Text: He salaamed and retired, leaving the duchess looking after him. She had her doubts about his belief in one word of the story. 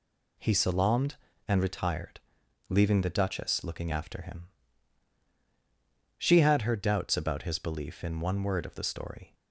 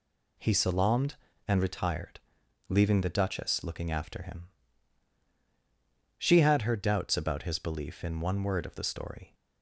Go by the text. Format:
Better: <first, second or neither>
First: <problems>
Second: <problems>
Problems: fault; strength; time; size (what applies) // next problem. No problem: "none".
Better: neither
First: none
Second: none